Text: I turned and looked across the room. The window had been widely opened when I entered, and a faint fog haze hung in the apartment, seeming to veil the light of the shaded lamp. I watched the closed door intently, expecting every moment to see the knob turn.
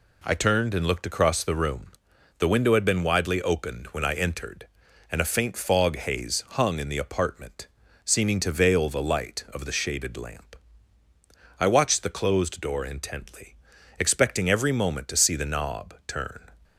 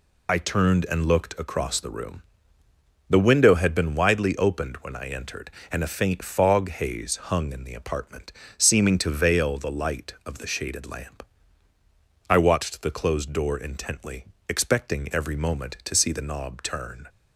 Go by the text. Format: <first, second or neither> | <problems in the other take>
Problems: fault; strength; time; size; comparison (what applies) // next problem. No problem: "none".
first | loses the start of "I"; at 0.2 s; 35 ms